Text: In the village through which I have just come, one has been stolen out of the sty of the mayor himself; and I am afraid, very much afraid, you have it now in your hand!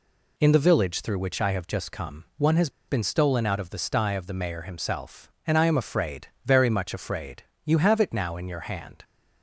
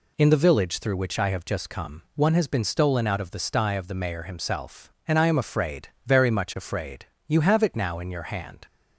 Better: second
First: pauses between "has" and "been"; slight; at 2.6 s; 0.19 s long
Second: none

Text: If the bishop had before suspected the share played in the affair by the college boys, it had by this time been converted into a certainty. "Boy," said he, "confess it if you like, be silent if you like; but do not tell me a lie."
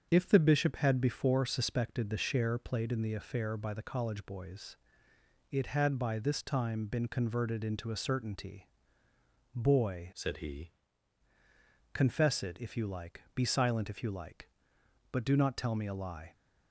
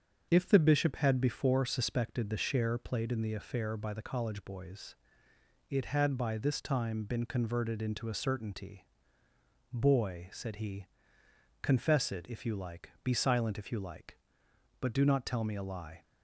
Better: second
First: starts louder than the rest; strong; until 1.1 s; 7 dB // changes voice from "said" to "he"; from 10.1 to 10.7 s; 0.6 s long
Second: starts louder than the rest; until 1.3 s; 7 dB

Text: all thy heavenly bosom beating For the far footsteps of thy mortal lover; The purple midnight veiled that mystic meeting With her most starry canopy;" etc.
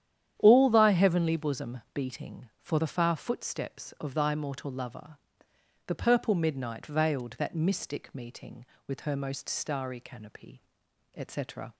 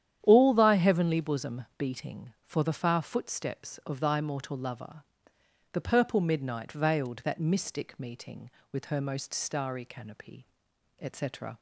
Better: neither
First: starts louder than the rest; strong; until 1.3 s; 10 dB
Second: starts louder than the rest; strong; until 1.2 s; 10 dB

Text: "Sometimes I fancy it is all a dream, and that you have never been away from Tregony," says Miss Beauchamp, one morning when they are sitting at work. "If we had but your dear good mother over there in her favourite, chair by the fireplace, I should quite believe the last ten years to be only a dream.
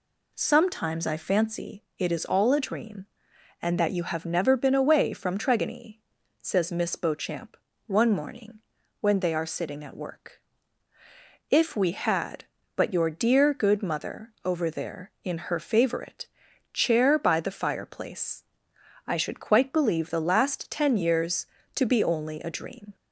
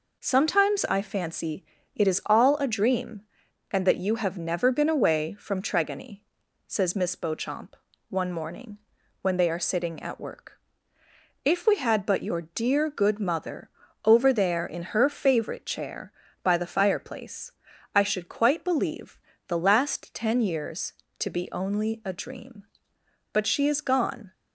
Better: first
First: pauses between "fancy" and "it"; slight; at 1.8 s; 0.16 s long // pauses between "morning" and "when"; at 8.5 s; 0.42 s long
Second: pauses between "fancy" and "it"; slight; at 1.6 s; 0.30 s long // pauses between "morning" and "when"; at 8.7 s; 0.42 s long // pauses between "mother" and "over"; at 13.6 s; 0.38 s long // pauses between "believe" and "the"; slight; at 19.1 s; 0.30 s long // goes on to say "But she is gone"; noticeable; from 23.3 s on; 1.0 s long

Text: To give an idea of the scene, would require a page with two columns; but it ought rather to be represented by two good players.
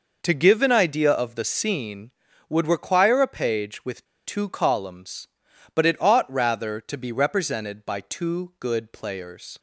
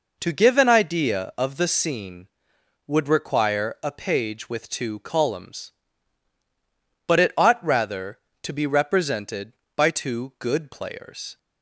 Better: second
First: pauses between "with" and "two"; slight; at 4.0 s; 0.20 s long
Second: none

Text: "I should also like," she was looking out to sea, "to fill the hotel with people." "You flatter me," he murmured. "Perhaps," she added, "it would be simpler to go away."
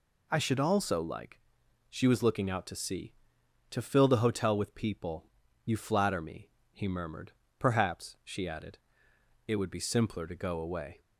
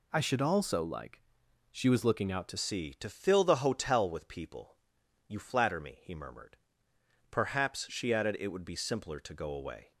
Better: first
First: none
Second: changes voice at "sea"; from 2.5 s on; 7.4 s long

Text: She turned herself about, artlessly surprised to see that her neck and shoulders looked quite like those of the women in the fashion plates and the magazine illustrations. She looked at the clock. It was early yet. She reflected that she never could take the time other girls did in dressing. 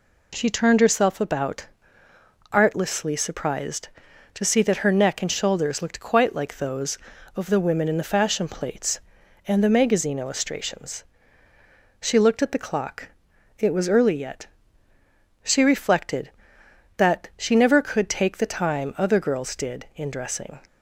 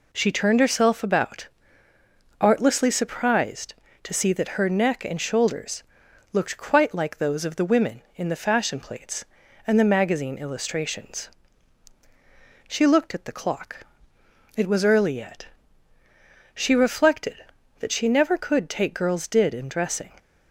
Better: first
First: none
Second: pauses between "shoulders" and "looked"; noticeable; at 5.8 s; 0.50 s long // skips "the time other"; at 18.9 s

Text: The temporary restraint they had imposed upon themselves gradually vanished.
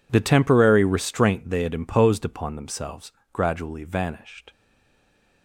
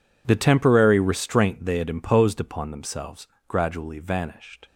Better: second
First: pauses between "themselves" and "gradually"; slight; at 3.1 s; 0.18 s long // stays silent after the last word; slight; from 4.5 s on; 0.9 s long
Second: pauses between "themselves" and "gradually"; slight; at 3.2 s; 0.18 s long

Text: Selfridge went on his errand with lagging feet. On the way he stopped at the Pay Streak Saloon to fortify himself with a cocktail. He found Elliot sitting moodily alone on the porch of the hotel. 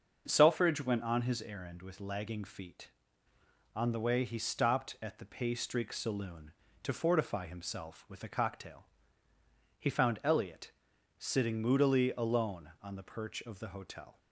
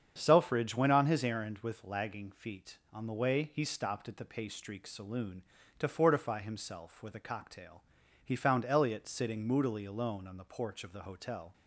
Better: second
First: starts louder than the rest; until 1.2 s; 6.5 dB // pauses between "Elliot" and "sitting"; noticeable; at 10.7 s; 0.46 s long // says "perch" for "porch"; at 13.0 s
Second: starts louder than the rest; strong; until 1.1 s; 7.5 dB

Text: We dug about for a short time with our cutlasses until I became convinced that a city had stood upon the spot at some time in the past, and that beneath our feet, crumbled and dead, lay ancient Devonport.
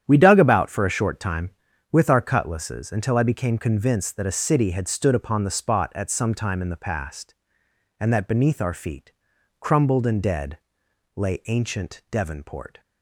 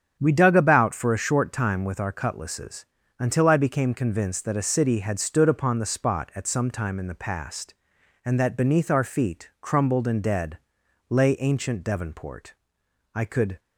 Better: first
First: starts louder than the rest; strong; until 1.0 s; 9.5 dB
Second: starts louder than the rest; strong; until 1.2 s; 8 dB // pauses between "cutlasses" and "until"; slight; at 2.8 s; 0.34 s long // goes on to say "I could"; slight; from 13.1 s on; 0.46 s long

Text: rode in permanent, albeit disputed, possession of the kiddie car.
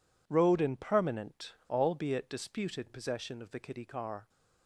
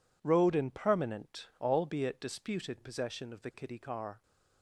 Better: neither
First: none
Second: none

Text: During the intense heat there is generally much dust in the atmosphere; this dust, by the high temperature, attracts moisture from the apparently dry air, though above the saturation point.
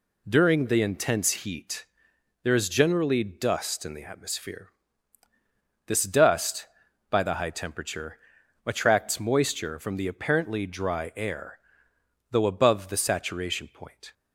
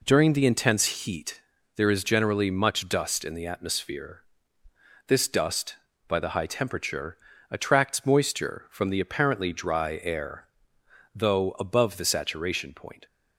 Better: second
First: pauses between "heat" and "there"; noticeable; at 1.8 s; 0.58 s long // skips "much"; at 3.2 s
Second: pauses between "heat" and "there"; slight; at 1.4 s; 0.36 s long

